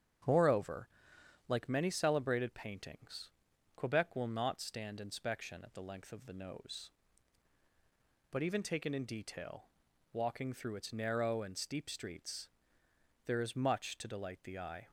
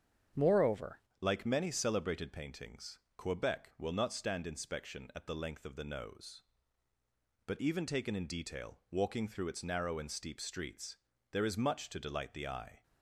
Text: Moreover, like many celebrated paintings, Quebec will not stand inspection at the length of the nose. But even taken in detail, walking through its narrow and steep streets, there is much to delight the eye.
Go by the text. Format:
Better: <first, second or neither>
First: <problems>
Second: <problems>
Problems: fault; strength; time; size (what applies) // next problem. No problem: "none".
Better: first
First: starts louder than the rest; strong; until 1.8 s; 8.5 dB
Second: starts louder than the rest; strong; until 1.5 s; 8 dB // changes voice at "like"; from 1.2 s on; 11.6 s long